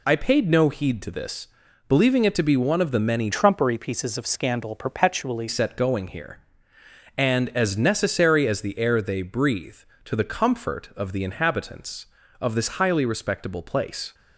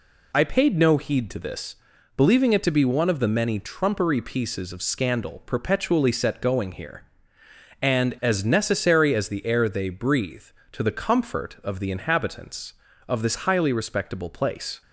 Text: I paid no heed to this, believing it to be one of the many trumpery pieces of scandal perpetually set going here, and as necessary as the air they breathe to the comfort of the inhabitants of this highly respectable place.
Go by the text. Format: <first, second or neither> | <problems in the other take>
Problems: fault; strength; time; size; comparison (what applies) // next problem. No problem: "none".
second | changes voice from "trumpery" to "perpetually"; from 3.3 to 5.4 s; 2.1 s long